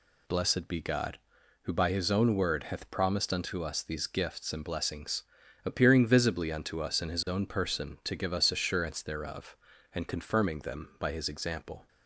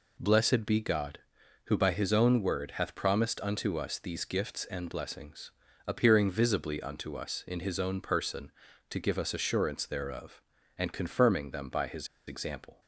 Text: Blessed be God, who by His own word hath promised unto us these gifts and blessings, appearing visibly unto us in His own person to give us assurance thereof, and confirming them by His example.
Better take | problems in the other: first | pauses between "His" and "example"; slight; at 12.0 s; 0.21 s long

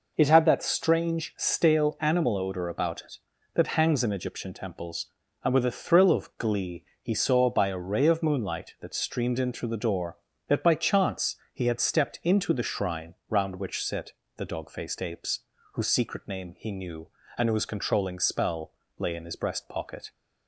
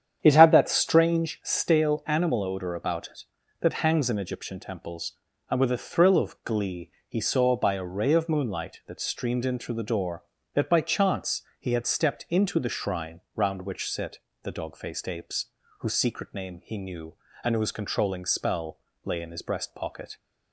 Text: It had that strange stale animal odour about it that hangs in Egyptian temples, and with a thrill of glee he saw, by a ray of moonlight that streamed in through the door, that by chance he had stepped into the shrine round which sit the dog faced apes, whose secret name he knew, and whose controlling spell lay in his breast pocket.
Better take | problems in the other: first | starts louder than the rest; strong; until 1.3 s; 9 dB // pauses between "glee" and "he"; slight; at 6.8 s; 0.18 s long; slight in the first // pauses between "chance" and "he"; slight; at 11.4 s; 0.18 s long; slight in the first // pauses between "sit" and "the"; slight; at 14.1 s; 0.24 s long; slight in the first // pauses between "spell" and "lay"; slight; at 18.7 s; 0.26 s long; slight in the first

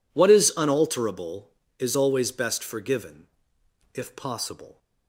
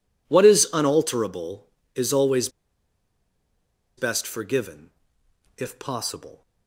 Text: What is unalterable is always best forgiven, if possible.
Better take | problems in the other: first | pauses between "always" and "best"; strong; at 2.4 s; 1.4 s long

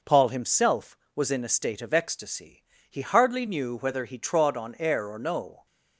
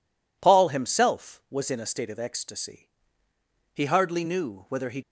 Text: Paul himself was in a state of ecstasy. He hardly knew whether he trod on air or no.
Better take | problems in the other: first | stops before "trod on air or no"; at 5.0 s

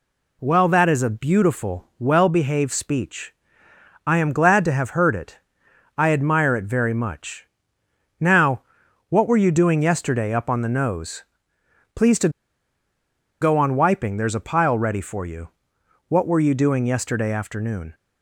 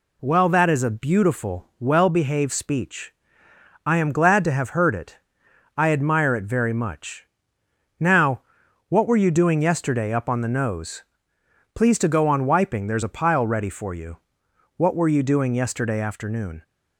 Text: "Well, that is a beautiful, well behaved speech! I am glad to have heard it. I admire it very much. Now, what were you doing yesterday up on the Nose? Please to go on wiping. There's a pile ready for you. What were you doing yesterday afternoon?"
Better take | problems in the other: second | pauses between "to" and "go"; at 12.2 s; 1.1 s long

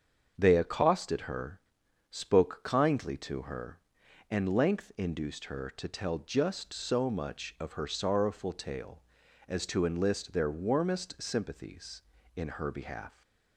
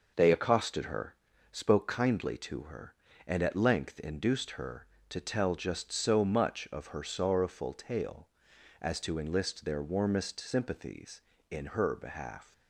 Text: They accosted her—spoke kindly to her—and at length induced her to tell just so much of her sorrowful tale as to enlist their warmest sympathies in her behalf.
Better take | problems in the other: second | starts louder than the rest; until 1.3 s; 7 dB // skips "at"; at 4.5 s

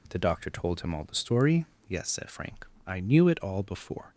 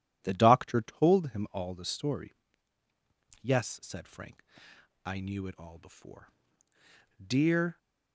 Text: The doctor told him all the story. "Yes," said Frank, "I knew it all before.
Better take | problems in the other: first | goes on to say "Dear"; from 7.1 s on; 0.58 s long

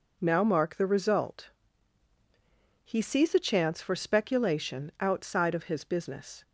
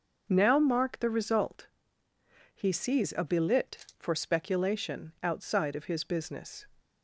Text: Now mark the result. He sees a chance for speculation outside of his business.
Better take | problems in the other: first | says "belit" for "chance"; at 3.2 s

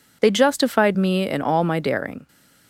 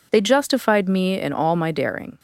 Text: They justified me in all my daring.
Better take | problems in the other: neither | none

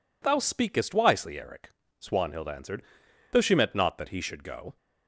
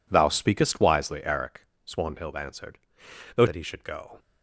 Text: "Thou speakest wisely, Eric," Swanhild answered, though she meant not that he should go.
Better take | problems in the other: first | skips "she meant not"; at 3.4 s

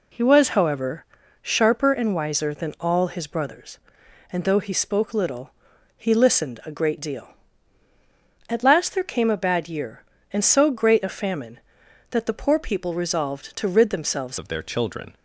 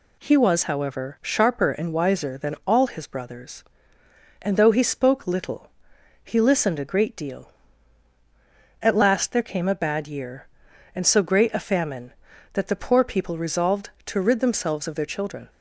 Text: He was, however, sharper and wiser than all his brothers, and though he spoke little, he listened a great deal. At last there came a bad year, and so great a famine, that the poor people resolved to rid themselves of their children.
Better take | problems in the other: second | changes voice at "of"; from 14.3 s on; 0.8 s long

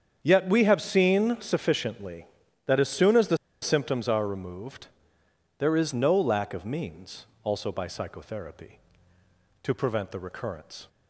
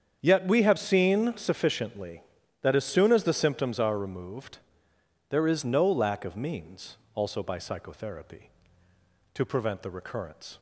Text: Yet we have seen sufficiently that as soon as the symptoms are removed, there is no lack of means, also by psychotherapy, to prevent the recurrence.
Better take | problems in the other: second | starts louder than the rest; strong; until 1.2 s; 8 dB; strong in the second // pauses between "the" and "symptoms"; slight; at 3.3 s; 0.24 s long

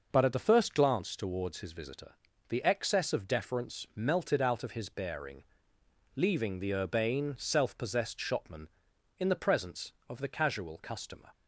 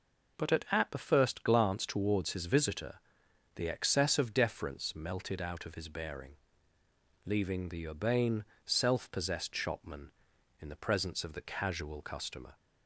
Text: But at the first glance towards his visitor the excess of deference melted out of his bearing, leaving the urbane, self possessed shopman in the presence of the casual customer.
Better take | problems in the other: first | says "at" twice; at 0.7 s // pauses between "visitor" and "the"; noticeable; at 2.9 s; 0.56 s long; slight in the first

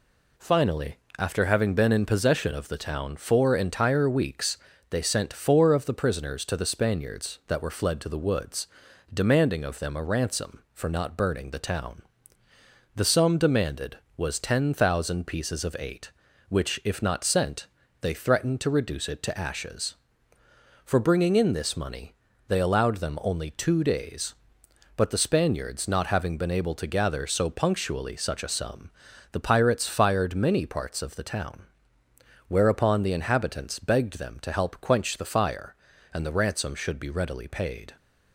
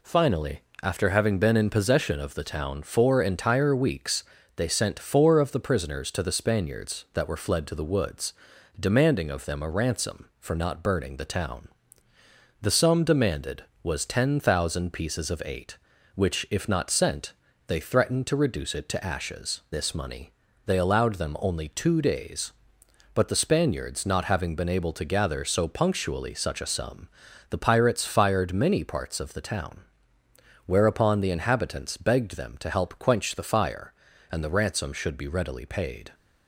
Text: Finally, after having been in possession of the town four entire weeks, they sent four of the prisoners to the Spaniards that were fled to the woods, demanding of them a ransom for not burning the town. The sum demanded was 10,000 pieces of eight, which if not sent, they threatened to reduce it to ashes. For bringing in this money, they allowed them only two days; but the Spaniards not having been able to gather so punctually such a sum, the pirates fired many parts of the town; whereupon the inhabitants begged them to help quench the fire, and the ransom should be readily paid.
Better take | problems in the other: first | skips "For bringing in"; at 19.6 s

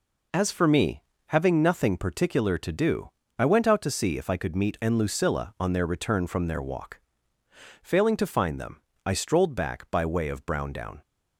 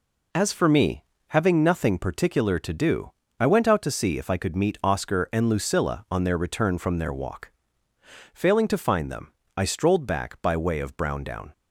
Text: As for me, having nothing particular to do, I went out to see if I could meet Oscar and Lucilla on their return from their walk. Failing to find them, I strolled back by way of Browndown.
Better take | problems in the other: second | skips "Oscar"; at 4.7 s

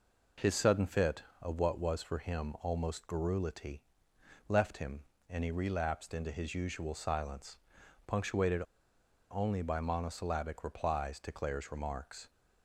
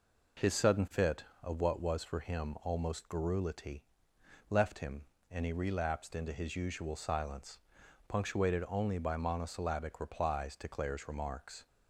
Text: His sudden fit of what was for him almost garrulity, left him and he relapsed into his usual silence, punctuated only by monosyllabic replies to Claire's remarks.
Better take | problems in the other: second | pauses between "punctuated" and "only"; noticeable; at 8.6 s; 0.67 s long

